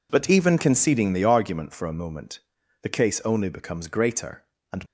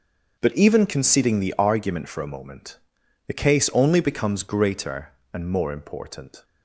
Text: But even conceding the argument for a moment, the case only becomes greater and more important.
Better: second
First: stops before "more important"; at 4.8 s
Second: none

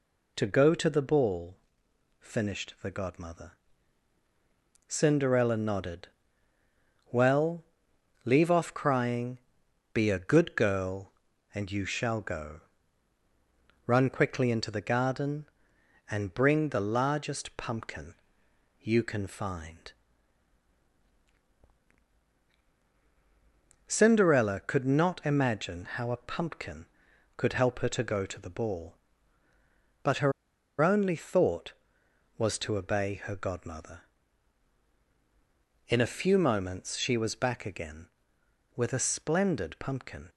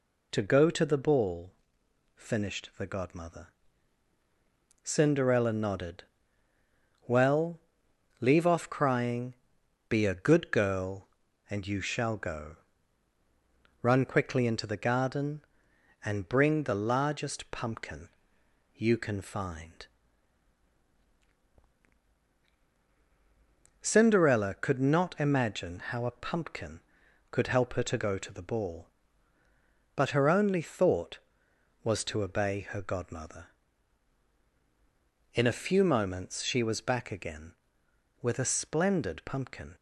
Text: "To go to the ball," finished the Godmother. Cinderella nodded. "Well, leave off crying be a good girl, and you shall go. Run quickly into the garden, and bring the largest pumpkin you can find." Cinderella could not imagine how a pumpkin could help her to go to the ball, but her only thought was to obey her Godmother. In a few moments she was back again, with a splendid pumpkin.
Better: second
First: pauses between "crying" and "be"; noticeable; at 9.3 s; 0.54 s long // pauses between "pumpkin" and "you"; noticeable; at 18.1 s; 0.66 s long // pauses between "her" and "only"; noticeable; at 30.3 s; 0.49 s long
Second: pauses between "crying" and "be"; noticeable; at 9.3 s; 0.54 s long // pauses between "pumpkin" and "you"; noticeable; at 18.0 s; 0.66 s long

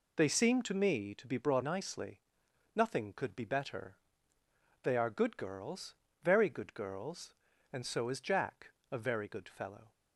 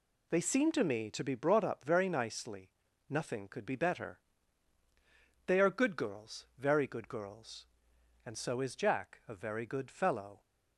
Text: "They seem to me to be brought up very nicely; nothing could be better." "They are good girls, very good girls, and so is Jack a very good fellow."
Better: second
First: skips "up very"; at 1.6 s // pauses between "Jack" and "a"; slight; at 8.7 s; 0.22 s long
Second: none

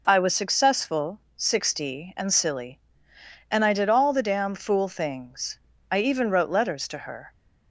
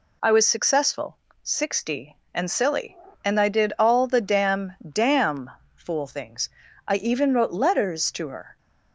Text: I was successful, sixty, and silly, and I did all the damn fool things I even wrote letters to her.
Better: first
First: pauses between "things" and "I"; slight; at 5.5 s; 0.32 s long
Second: says "damn" twice; at 4.9 s // pauses between "things" and "I"; slight; at 6.4 s; 0.36 s long

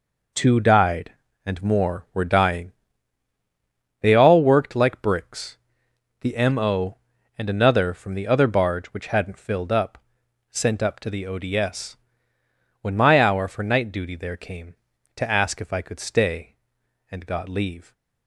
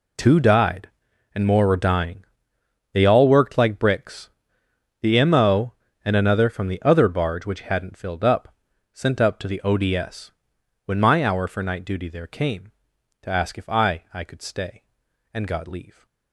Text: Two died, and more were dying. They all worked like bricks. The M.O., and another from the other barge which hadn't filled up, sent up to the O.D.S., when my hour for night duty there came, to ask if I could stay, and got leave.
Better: first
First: none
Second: says "I" twice; at 14.1 s

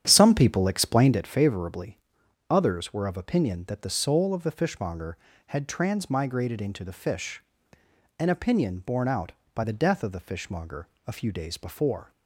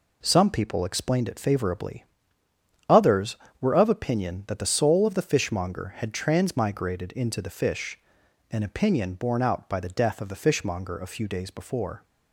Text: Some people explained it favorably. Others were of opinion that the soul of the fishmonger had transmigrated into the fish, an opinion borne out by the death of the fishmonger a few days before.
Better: second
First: starts louder than the rest; strong; until 1.2 s; 9 dB // pauses between "fishmonger" and "a"; slight; at 10.8 s; 0.20 s long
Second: none

